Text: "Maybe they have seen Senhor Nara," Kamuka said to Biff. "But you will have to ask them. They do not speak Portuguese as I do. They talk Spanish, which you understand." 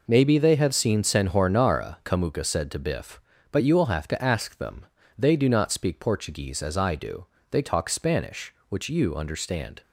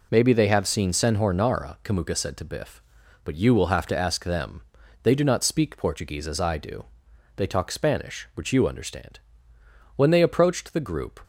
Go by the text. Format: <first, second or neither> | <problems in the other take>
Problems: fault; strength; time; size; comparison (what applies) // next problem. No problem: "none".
first | goes on to say "When they approached the group"; noticeable; from 9.9 s on; 1.2 s long